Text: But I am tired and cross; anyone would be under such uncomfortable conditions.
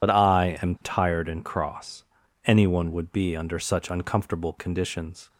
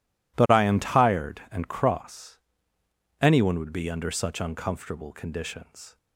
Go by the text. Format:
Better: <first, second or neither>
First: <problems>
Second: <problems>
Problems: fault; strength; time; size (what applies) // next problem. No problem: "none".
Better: second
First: loses the start of "But"; at 0.0 s; 60 ms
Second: none